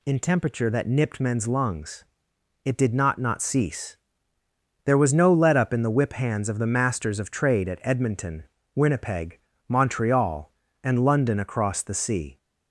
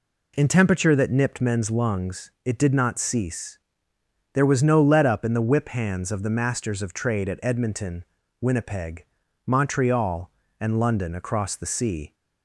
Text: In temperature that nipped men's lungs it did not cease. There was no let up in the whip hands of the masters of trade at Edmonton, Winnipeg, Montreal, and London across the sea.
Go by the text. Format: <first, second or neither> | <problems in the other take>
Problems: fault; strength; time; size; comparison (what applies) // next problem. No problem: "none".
second | pauses between "lungs" and "it"; noticeable; at 2.0 s; 0.60 s long // says "not" twice; at 3.1 s